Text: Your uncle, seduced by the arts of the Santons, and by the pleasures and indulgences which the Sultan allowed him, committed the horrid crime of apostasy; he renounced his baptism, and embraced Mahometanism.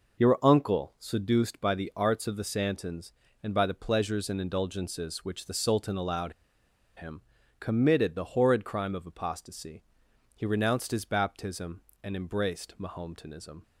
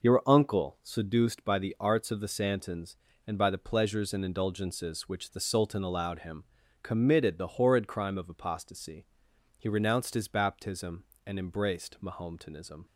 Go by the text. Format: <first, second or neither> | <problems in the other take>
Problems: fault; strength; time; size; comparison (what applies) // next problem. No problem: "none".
second | pauses between "allowed" and "him"; noticeable; at 6.3 s; 0.63 s long